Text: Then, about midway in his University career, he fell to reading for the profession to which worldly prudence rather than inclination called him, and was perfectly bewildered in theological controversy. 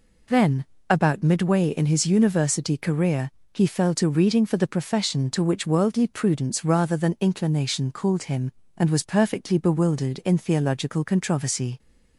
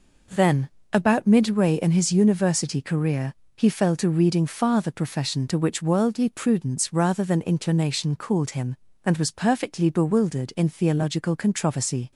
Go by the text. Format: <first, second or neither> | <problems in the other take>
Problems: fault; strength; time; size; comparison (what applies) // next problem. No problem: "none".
first | says "far" for "for"; at 4.4 s